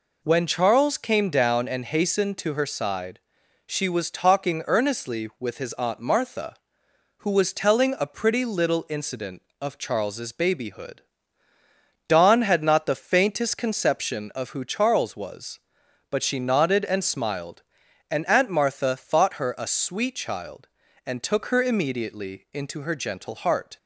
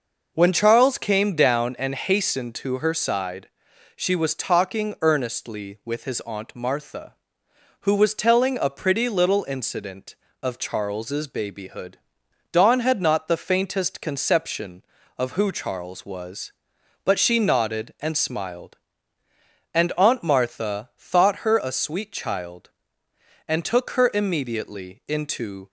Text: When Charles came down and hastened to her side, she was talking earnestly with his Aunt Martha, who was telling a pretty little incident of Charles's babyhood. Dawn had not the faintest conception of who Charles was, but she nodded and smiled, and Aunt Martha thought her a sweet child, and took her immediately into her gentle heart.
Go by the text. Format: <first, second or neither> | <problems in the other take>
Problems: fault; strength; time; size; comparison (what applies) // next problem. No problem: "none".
first | stops before "her gentle heart"; at 25.6 s